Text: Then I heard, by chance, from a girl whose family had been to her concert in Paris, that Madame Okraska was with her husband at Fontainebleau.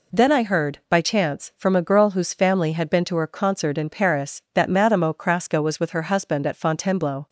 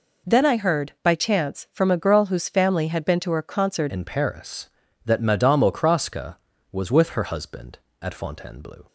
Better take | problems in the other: first | changes voice at "in"; from 3.9 s on; 4.9 s long

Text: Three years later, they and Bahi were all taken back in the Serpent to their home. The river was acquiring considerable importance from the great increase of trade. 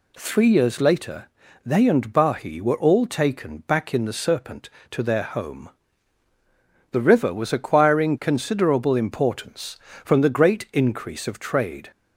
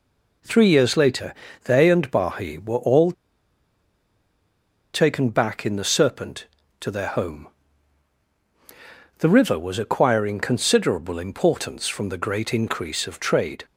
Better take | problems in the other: first | pauses between "all" and "taken"; strong; at 3.1 s; 1.8 s long

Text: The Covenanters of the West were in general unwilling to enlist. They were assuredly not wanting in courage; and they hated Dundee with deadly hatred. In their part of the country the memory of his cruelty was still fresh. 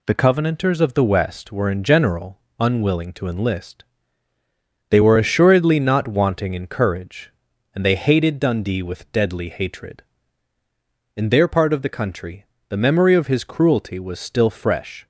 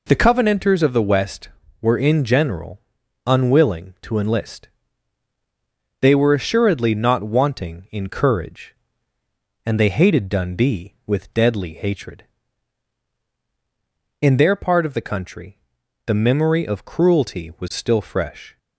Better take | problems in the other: first | pauses between "general" and "unwilling"; noticeable; at 2.7 s; 0.46 s long; slight in the first // pauses between "country" and "the"; noticeable; at 15.5 s; 0.48 s long; slight in the first // skips "his"; at 16.8 s

